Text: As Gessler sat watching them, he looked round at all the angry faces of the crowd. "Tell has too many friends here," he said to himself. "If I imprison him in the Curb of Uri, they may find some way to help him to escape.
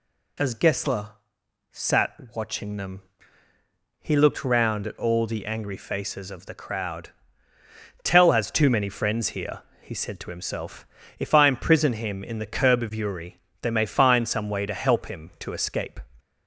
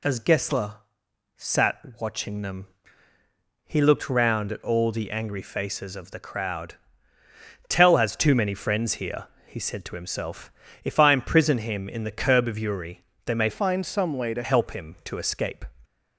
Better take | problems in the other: first | pauses between "Gessler" and "sat"; noticeable; at 0.7 s; 0.62 s long; noticeable in the first // pauses between "sat" and "watching"; slight; at 1.7 s; 0.18 s long; slight in the first // changes voice from "find" to "to"; from 13.4 to 14.4 s; 1.0 s long

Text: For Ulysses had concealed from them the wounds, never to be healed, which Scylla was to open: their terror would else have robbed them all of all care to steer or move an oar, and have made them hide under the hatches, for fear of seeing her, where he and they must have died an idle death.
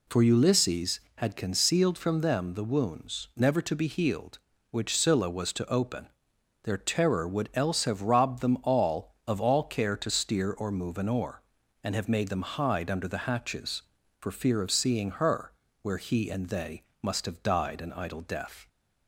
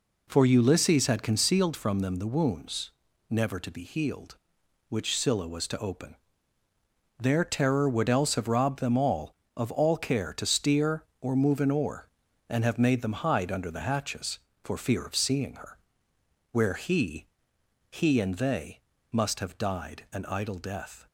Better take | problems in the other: first | says "he" twice; at 17.8 s // pauses between "they" and "must"; slight; at 18.8 s; 0.32 s long; slight in the first

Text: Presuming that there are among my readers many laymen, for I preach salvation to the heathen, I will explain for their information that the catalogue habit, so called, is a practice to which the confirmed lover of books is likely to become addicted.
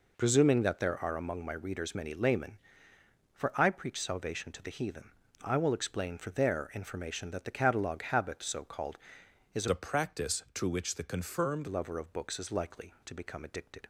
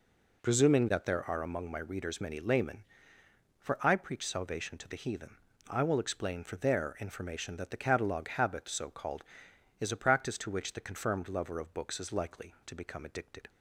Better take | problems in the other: second | changes voice from "a" to "confirmed"; from 9.6 to 11.6 s; 2.0 s long

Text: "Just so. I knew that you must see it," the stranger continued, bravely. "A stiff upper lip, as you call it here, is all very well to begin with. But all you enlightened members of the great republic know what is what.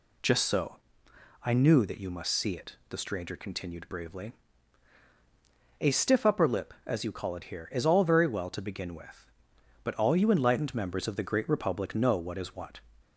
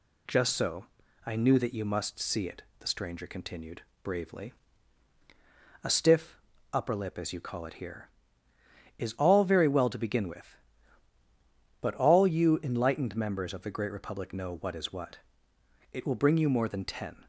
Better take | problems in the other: first | pauses between "stiff" and "upper"; slight; at 6.4 s; 0.32 s long // goes on to say "It will bring you more than ten"; from 15.9 s on; 1.3 s long

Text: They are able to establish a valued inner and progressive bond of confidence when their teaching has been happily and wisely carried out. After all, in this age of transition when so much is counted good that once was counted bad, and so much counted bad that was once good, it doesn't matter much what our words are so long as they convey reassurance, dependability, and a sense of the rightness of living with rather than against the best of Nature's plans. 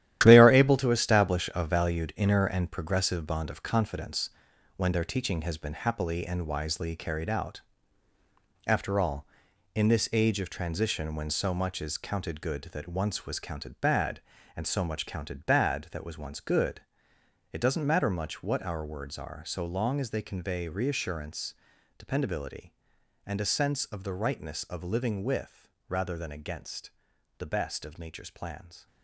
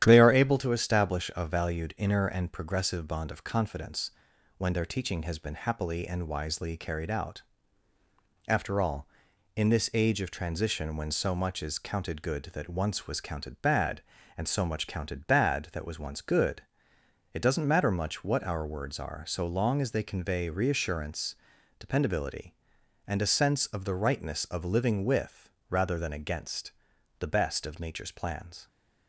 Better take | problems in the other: second | gets quieter; strong; throughout; 10 dB // starts louder than the rest; strong; until 1.2 s; 12 dB; strong in the second // pauses between "confidence" and "when"; noticeable; at 4.2 s; 0.46 s long; noticeable in the second // pauses between "with" and "rather"; slight; at 25.6 s; 0.20 s long; slight in the second // pauses between "against" and "the"; noticeable; at 26.9 s; 0.46 s long; noticeable in the second

